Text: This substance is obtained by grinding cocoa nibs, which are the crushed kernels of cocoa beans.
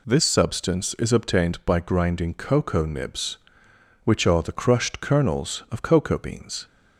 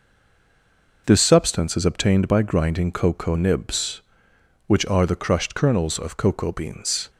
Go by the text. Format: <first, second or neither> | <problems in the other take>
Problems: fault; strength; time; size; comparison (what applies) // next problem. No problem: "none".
first | stays silent before the first word; until 1.0 s; 1.0 s long